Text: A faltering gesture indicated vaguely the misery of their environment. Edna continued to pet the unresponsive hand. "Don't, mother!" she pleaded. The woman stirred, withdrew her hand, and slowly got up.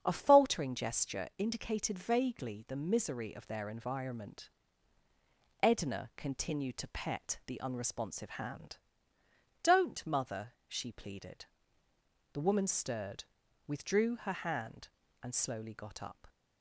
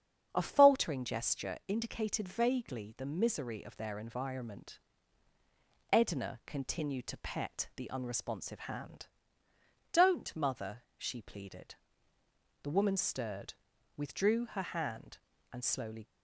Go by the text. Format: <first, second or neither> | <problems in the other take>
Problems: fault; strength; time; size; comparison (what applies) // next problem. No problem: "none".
first | starts louder than the rest; strong; until 1.3 s; 8 dB; strong in the first // stops before "got up"; at 16.0 s